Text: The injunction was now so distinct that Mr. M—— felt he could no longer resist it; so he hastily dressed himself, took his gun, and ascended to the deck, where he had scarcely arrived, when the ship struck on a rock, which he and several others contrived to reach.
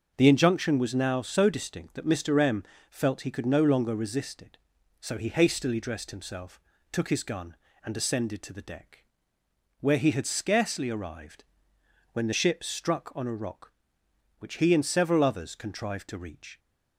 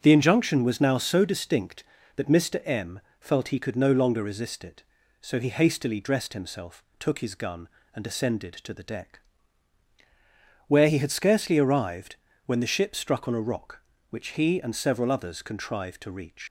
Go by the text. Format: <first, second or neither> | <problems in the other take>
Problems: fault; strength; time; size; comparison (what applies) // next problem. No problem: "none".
first | starts louder than the rest; strong; until 1.0 s; 7.5 dB; also in the first // leaves "reach" unfinished; at 16.4 s; 125 ms